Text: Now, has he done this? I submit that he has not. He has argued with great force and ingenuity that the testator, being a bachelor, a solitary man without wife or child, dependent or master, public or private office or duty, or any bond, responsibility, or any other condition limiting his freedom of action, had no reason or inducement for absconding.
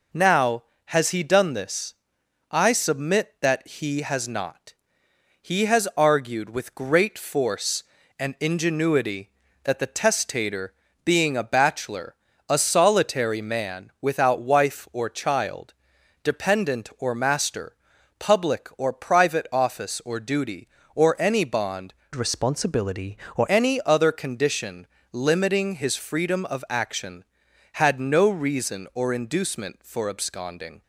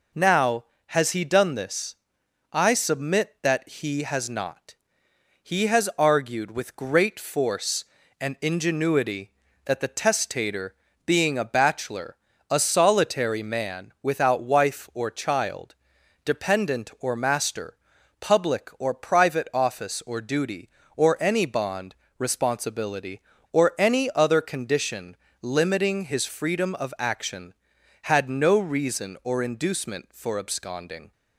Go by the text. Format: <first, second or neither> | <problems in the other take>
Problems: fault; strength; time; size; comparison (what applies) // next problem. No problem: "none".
second | changes voice from "responsibility" to "or"; from 22.1 to 23.4 s; 1.3 s long // pauses between "condition" and "limiting"; slight; at 24.8 s; 0.26 s long; slight in the second